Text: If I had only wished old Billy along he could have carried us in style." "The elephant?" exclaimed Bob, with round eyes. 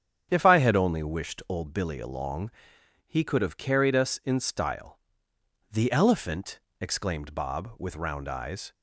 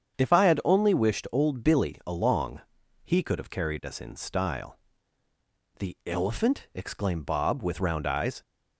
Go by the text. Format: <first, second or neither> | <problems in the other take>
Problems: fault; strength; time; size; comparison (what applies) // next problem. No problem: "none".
neither | starts louder than the rest; strong; the same in both // pauses between "along" and "he"; noticeable; the same in both